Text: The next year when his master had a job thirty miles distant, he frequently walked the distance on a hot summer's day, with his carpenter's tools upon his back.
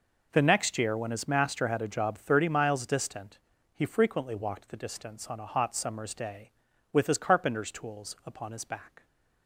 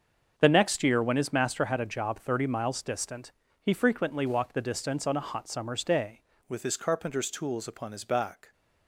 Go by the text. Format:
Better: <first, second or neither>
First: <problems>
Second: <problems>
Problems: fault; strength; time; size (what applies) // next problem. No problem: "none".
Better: first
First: none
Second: starts louder than the rest; until 1.3 s; 6.5 dB // changes voice at "with"; from 6.4 s on; 2.1 s long